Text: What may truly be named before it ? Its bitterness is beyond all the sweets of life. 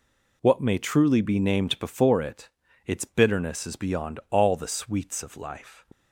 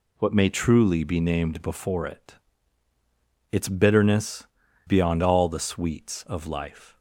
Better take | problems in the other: first | skips "is"; at 4.6 s

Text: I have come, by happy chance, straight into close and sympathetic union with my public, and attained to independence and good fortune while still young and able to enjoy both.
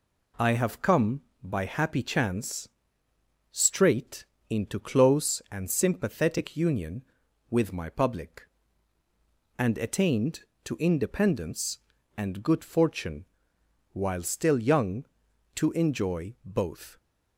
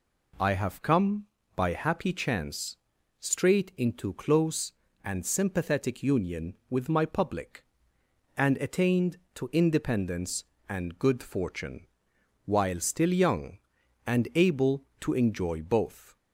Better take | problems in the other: second | pauses between "straight" and "into"; slight; at 4.2 s; 0.26 s long // pauses between "fortune" and "while"; noticeable; at 13.2 s; 0.66 s long; noticeable in the second // skips "and able"; at 15.2 s

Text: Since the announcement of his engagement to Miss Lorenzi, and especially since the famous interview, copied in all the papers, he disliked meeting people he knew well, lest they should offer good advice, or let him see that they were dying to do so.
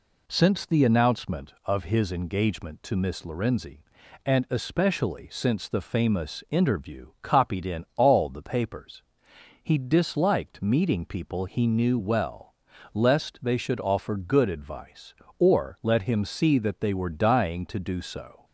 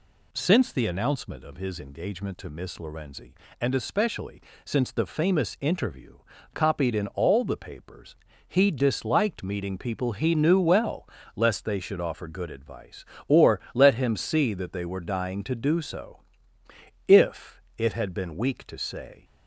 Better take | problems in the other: first | pauses between "especially" and "since"; slight; at 4.3 s; 0.24 s long // goes on to say "If it had been weak to say"; strong; from 17.0 s on; 2.1 s long

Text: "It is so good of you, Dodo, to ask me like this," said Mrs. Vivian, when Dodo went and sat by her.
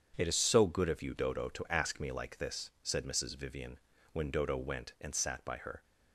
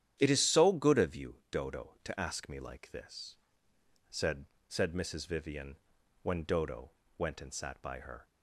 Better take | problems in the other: first | starts louder than the rest; strong; until 1.2 s; 10 dB; strong in the first // says "said" twice; at 4.6 s // pauses between "Dodo" and "went"; slight; at 6.8 s; 0.28 s long

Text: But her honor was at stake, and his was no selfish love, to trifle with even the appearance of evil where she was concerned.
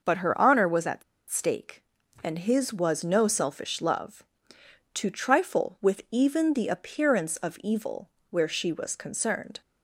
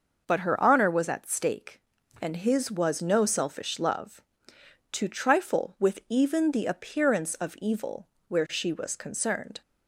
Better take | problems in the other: second | pauses between "at" and "stake"; slight; at 1.0 s; 0.27 s long // pauses between "evil" and "where"; slight; at 8.0 s; 0.22 s long; slight in the second

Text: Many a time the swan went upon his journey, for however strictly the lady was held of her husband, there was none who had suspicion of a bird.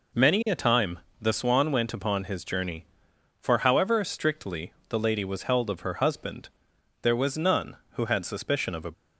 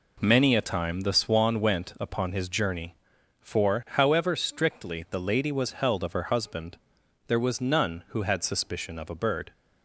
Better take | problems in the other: second | pauses between "time" and "the"; slight; at 0.9 s; 0.24 s long // pauses between "strictly" and "the"; slight; at 4.7 s; 0.18 s long // stops before "bird"; at 8.9 s

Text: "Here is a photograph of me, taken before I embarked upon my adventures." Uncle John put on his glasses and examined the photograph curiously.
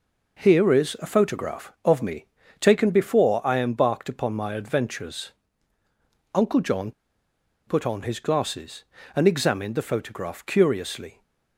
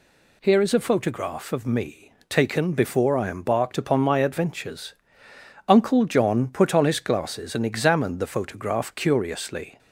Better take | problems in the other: second | pauses between "John" and "put"; noticeable; at 6.9 s; 0.75 s long

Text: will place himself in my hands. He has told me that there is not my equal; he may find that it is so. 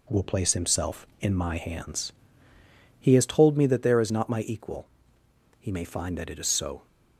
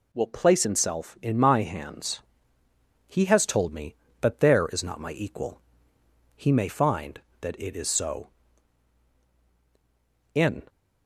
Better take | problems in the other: first | goes on to say "In"; slight; from 10.3 s on; 0.34 s long

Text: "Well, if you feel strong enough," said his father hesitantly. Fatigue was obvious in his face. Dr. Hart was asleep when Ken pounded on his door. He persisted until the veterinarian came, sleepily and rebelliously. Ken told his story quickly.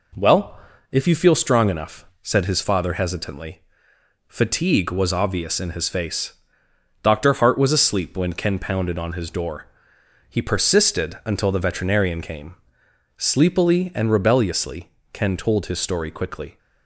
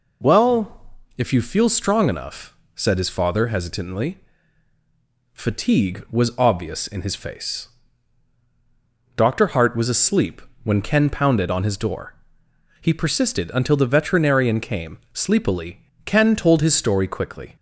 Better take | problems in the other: first | pauses between "asleep" and "when"; slight; at 10.3 s; 0.22 s long // skips "and rebelliously"; at 15.9 s

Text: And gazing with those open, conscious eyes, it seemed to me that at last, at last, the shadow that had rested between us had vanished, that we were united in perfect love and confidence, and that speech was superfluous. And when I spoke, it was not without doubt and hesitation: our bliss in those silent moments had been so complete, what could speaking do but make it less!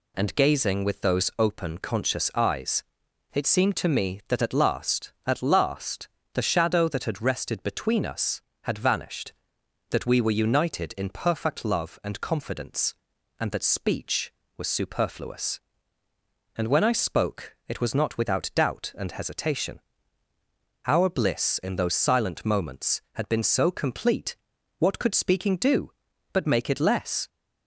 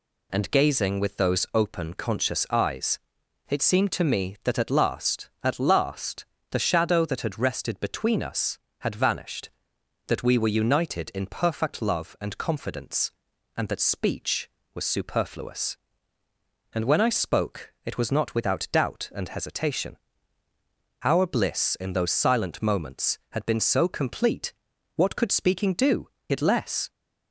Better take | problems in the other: first | skips "but make"; at 26.1 s

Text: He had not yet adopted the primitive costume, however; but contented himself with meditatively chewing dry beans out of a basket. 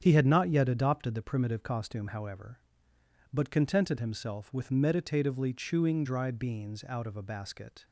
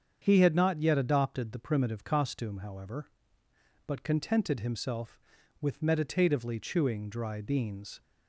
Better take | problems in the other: first | starts louder than the rest; strong; until 1.2 s; 7.5 dB; strong in the first // stops before "out of a basket"; at 8.0 s

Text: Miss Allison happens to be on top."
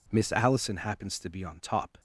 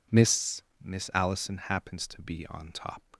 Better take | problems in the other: first | says "Miss" twice; at 0.8 s

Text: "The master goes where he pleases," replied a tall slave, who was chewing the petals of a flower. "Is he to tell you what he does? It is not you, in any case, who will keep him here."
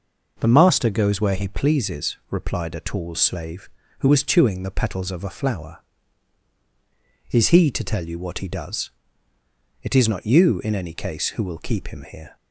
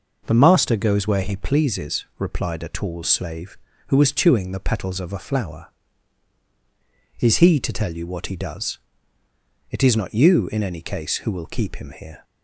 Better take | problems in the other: neither | none

